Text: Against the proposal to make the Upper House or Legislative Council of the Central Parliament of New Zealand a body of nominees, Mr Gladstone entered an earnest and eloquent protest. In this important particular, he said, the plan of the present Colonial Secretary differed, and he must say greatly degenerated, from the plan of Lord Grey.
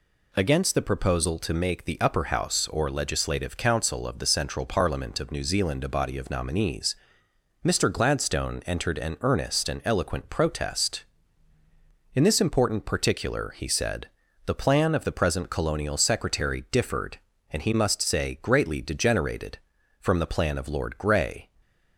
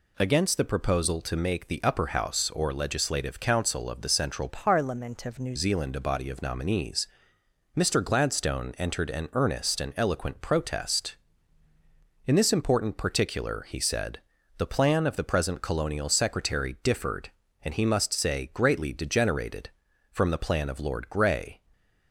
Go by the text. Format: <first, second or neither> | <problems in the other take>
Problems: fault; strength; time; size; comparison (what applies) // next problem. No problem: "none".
first | changes voice from "Parliament" to "New"; from 4.4 to 5.5 s; 1.1 s long